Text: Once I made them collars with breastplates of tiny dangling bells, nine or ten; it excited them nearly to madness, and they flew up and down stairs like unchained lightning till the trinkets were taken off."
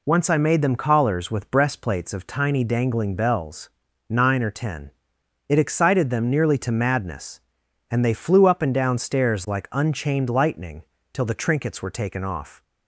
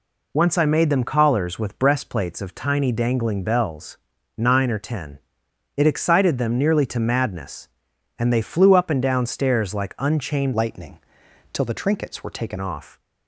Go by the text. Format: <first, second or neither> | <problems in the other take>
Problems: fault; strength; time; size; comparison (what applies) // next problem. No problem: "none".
first | changes voice from "lightning" to "taken"; from 10.5 to 12.5 s; 2.0 s long // pauses between "lightning" and "till"; noticeable; at 10.9 s; 0.54 s long; slight in the first